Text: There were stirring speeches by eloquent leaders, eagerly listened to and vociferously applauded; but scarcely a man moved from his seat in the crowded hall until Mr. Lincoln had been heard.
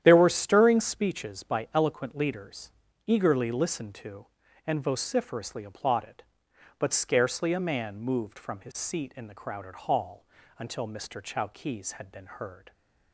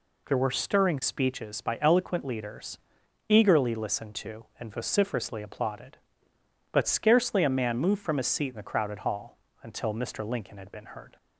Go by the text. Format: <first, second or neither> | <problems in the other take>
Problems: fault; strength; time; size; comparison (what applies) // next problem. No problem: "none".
second | starts louder than the rest; strong; until 1.0 s; 10.5 dB // pauses between "hall" and "until"; slight; at 10.2 s; 0.34 s long; slight in the second // says "Chowkees" for "Lincoln"; at 11.1 s